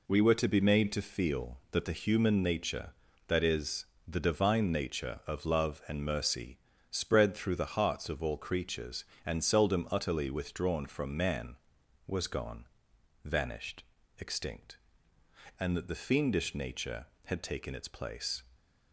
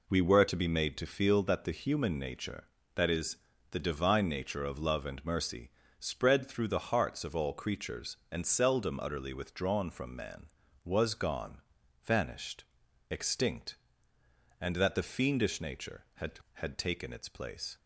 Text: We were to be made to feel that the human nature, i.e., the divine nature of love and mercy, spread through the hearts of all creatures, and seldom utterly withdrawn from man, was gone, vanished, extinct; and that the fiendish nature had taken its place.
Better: first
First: none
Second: says "had" twice; at 16.5 s

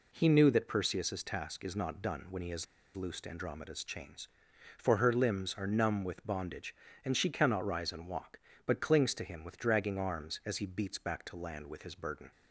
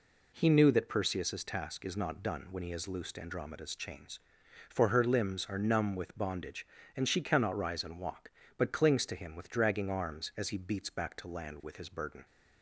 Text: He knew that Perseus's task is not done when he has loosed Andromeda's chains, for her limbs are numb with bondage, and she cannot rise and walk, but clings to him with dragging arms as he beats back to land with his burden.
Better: second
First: pauses between "has" and "loosed"; slight; at 2.6 s; 0.31 s long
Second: none

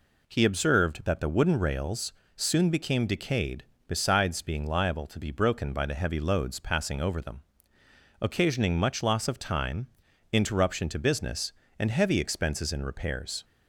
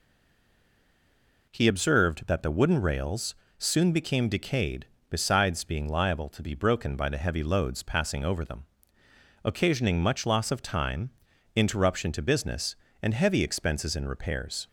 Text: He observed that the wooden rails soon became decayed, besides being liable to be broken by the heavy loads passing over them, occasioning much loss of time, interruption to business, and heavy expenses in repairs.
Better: first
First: pauses between "rails" and "soon"; slight; at 2.1 s; 0.22 s long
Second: stays silent before the first word; noticeable; until 1.4 s; 1.4 s long // pauses between "rails" and "soon"; slight; at 3.3 s; 0.22 s long

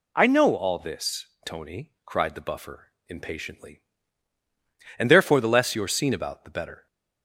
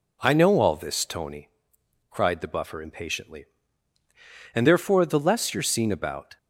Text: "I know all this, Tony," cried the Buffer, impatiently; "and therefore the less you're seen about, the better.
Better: first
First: none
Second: stops before "the better"; at 6.3 s

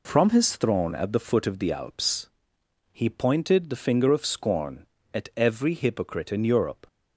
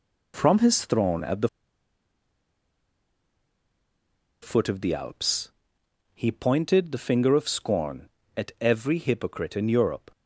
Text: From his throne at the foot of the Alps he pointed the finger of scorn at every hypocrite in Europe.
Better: first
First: pauses between "Alps" and "he"; noticeable; at 2.2 s; 0.64 s long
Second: pauses between "the" and "foot"; strong; at 1.4 s; 2.9 s long // pauses between "Alps" and "he"; noticeable; at 5.5 s; 0.64 s long

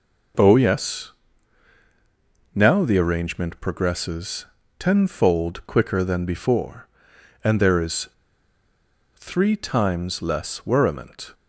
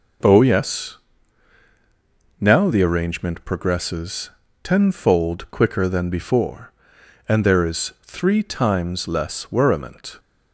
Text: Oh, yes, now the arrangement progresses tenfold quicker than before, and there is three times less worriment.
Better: second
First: pauses between "progresses" and "tenfold"; slight; at 4.4 s; 0.34 s long // pauses between "is" and "three"; at 8.0 s; 1.0 s long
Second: pauses between "progresses" and "tenfold"; slight; at 4.2 s; 0.34 s long

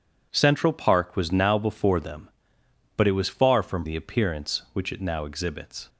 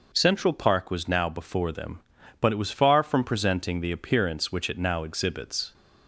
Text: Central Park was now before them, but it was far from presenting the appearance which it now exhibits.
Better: second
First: skips "presenting"; at 3.8 s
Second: none

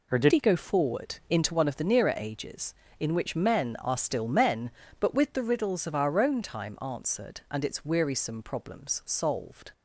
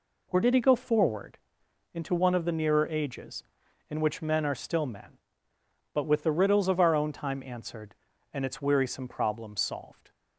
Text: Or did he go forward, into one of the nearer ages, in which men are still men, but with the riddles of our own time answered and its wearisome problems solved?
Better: second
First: changes voice at "he"; from 0.3 s on; 9.4 s long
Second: none

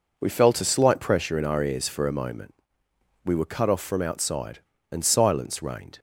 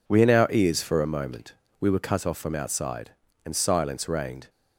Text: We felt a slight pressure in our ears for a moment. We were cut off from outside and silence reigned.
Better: first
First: none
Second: skips "felt a slight pressure"; at 0.2 s

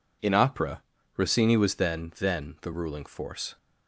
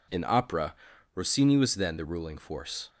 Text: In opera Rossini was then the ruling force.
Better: second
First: pauses between "opera" and "Rossini"; slight; at 0.8 s; 0.34 s long // says "then" twice; at 2.1 s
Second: pauses between "opera" and "Rossini"; at 0.7 s; 0.40 s long

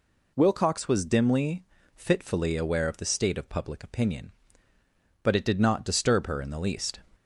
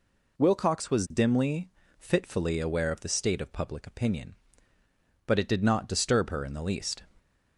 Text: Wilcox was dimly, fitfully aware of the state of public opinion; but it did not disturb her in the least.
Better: neither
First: none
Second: none

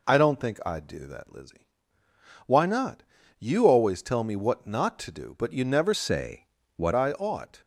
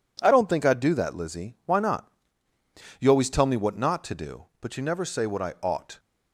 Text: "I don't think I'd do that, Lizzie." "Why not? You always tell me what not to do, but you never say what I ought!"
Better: second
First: changes voice from "say" to "what"; from 5.9 to 6.9 s; 1.0 s long // pauses between "say" and "what"; slight; at 6.4 s; 0.30 s long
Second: none

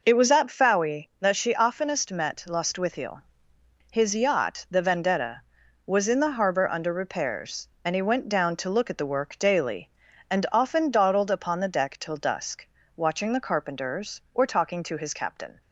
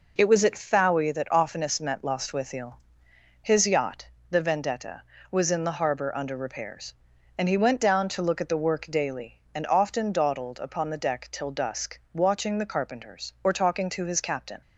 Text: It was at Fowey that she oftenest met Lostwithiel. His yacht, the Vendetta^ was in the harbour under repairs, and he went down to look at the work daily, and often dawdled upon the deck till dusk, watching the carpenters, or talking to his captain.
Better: first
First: none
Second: skips "she"; at 1.3 s

